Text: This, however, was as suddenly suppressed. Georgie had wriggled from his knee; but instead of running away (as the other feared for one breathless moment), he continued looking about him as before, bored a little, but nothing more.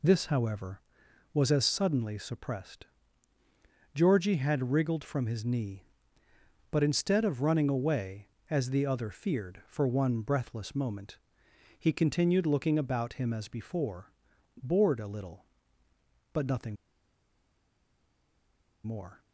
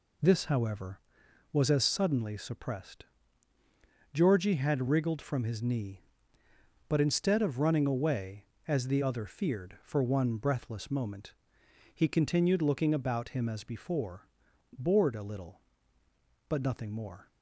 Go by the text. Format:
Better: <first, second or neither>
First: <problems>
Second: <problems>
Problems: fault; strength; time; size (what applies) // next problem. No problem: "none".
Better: second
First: pauses between "nothing" and "more"; strong; at 16.7 s; 2.0 s long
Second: none